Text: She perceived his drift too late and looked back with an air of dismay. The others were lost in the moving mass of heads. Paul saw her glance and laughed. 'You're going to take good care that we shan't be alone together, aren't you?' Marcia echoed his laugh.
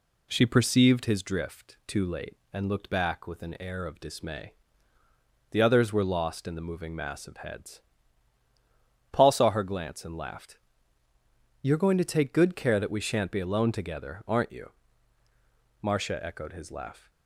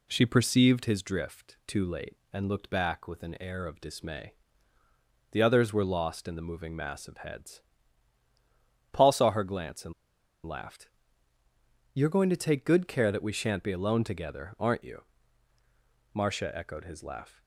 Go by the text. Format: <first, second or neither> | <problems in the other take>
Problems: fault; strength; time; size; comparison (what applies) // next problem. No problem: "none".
first | pauses between "and" and "laughed"; noticeable; at 9.9 s; 0.52 s long